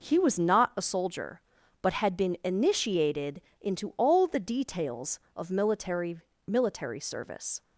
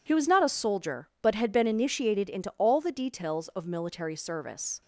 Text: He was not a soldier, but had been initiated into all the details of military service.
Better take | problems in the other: second | pauses between "initiated" and "into"; slight; at 3.3 s; 0.20 s long // says "military" twice; at 6.4 s

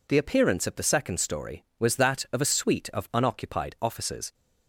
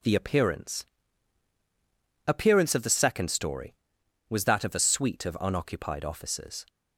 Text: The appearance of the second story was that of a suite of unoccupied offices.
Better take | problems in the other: first | says "appearance" twice; at 2.2 s

